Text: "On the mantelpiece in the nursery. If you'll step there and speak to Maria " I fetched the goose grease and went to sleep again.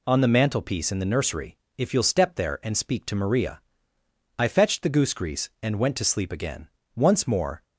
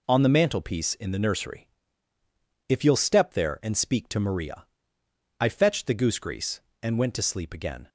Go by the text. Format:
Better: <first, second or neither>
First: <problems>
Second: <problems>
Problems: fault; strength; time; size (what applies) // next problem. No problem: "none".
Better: second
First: goes on to say "Once more"; noticeable; from 6.9 s on; 0.70 s long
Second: none